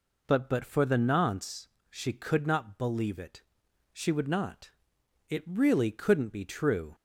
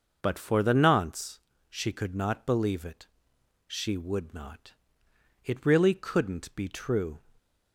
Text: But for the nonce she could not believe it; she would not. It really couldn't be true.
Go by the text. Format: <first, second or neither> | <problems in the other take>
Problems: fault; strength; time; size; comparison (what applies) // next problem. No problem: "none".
second | says "But" twice; at 0.4 s // pauses between "nonce" and "she"; slight; at 1.6 s; 0.22 s long; slight in the second